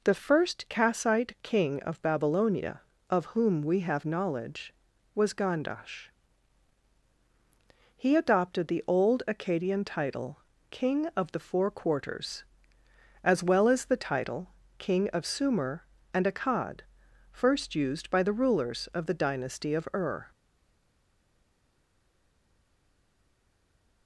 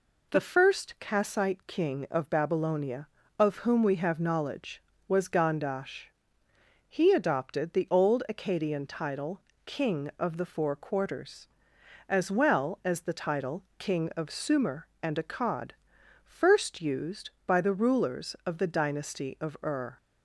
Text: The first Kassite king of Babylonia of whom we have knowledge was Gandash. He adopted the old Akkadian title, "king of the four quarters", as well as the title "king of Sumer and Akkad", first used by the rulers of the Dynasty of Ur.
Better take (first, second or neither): second